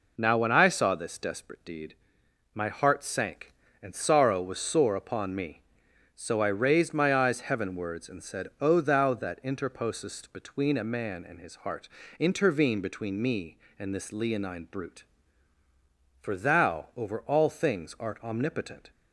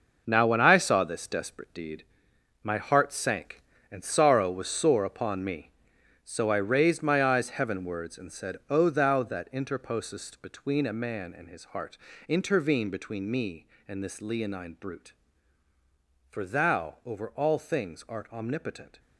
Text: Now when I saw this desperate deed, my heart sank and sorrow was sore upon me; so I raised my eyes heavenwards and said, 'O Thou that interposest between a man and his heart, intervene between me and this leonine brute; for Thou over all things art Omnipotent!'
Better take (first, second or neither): first